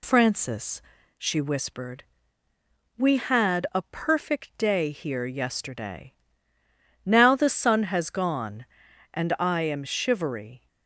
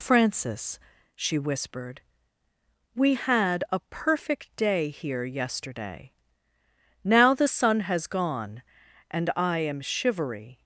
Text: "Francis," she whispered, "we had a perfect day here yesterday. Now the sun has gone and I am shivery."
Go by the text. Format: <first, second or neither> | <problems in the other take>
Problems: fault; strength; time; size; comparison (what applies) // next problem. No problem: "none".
neither | none